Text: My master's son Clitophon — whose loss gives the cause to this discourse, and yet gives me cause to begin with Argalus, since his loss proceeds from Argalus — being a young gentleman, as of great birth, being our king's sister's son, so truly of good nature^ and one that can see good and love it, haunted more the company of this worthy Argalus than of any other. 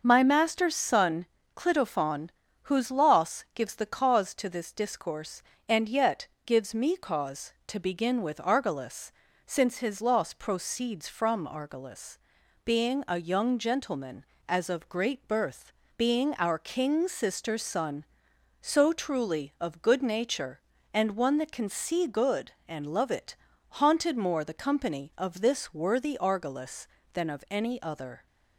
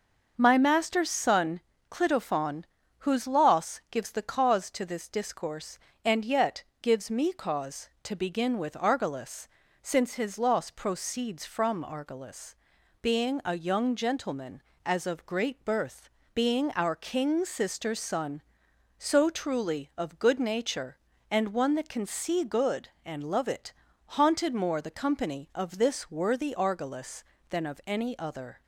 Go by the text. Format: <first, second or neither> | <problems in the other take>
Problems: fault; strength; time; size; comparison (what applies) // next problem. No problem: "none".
neither | starts louder than the rest; noticeable; the same in both // pauses between "son" and "Clitophon"; slight; the same in both // pauses between "yet" and "gives"; slight; the same in both